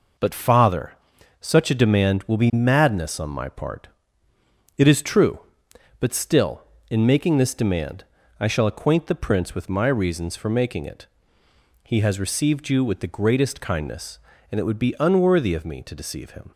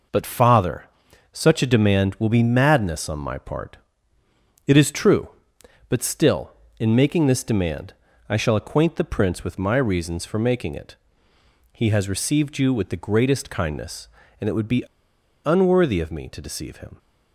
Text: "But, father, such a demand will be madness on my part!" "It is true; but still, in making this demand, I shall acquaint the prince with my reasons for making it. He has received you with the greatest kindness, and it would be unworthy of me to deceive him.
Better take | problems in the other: first | pauses between "be" and "unworthy"; noticeable; at 14.8 s; 0.61 s long

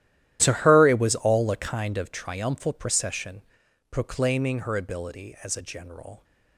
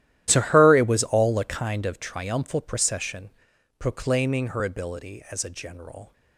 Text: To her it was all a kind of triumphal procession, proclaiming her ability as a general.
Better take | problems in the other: neither | starts louder than the rest; strong; the same in both

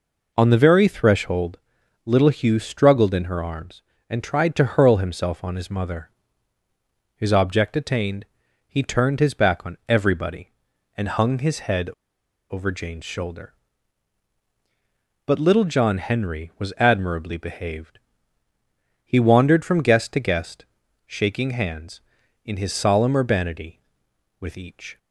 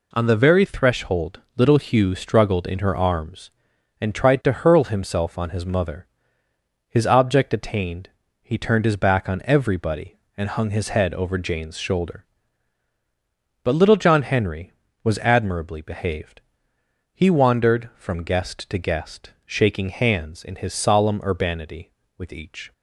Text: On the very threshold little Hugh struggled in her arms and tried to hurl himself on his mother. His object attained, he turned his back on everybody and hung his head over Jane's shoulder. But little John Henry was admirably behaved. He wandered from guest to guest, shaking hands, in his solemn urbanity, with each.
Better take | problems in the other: second | pauses between "threshold" and "little"; noticeable; at 1.5 s; 0.48 s long; slight in the second // pauses between "head" and "over"; noticeable; at 11.9 s; 0.59 s long

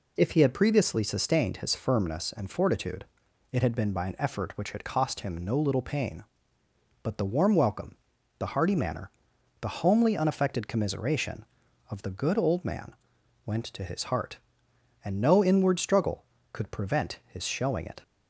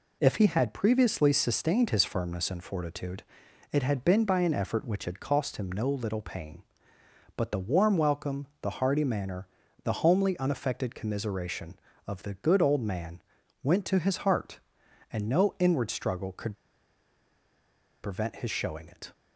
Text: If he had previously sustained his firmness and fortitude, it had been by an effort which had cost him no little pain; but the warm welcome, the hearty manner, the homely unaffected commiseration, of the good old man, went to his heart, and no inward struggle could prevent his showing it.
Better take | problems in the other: first | pauses between "could" and "prevent"; strong; at 16.5 s; 1.4 s long

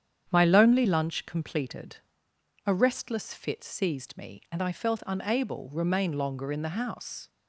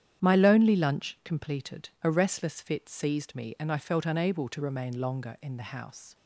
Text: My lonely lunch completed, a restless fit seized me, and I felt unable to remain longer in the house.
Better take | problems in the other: second | starts louder than the rest; strong; until 1.3 s; 9 dB; strong in the second // skips "to"; at 5.7 s

